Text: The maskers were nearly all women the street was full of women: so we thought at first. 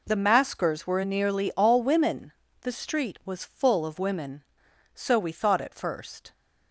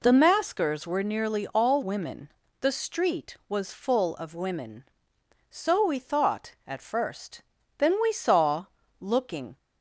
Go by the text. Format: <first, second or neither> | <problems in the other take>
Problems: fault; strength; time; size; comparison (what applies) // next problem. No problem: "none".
first | pauses between "women" and "the"; slight; at 2.3 s; 0.30 s long; slight in the first // goes on to say "Then we saw looking"; strong; from 7.7 s on; 1.8 s long